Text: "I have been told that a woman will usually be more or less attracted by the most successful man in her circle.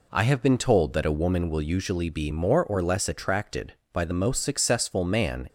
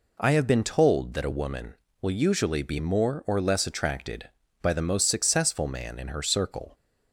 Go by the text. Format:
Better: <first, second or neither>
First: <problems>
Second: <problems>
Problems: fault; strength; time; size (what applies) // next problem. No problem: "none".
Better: second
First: stops before "in her circle"; at 5.4 s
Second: none